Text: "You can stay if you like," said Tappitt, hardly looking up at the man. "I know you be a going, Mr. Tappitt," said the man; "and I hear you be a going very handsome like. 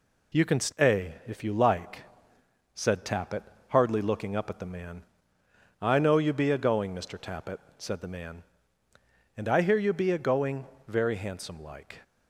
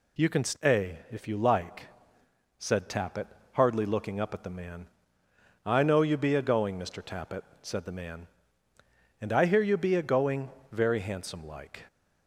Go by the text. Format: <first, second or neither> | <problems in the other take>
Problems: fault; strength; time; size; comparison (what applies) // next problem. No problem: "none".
second | gets quieter; slight; throughout; 2.5 dB // pauses between "going" and "very"; slight; at 10.6 s; 0.22 s long; slight in the second